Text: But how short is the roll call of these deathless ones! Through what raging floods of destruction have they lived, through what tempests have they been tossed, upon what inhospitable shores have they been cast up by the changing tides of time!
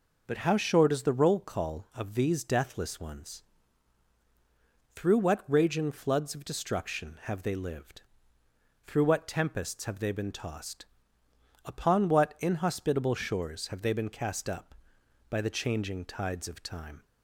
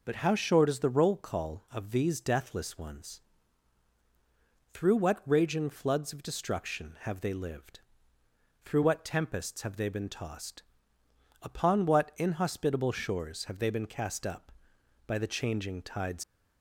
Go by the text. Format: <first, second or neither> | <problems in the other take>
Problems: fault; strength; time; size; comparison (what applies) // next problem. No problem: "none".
first | stops before "of time"; at 16.2 s